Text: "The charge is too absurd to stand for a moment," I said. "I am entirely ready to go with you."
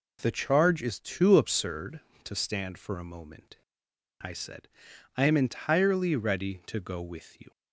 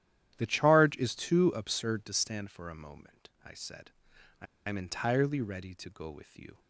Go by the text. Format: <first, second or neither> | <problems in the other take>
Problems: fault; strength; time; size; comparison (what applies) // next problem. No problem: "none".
first | starts louder than the rest; strong; until 1.3 s; 11.5 dB // pauses between "I" and "am"; slight; at 4.4 s; 0.22 s long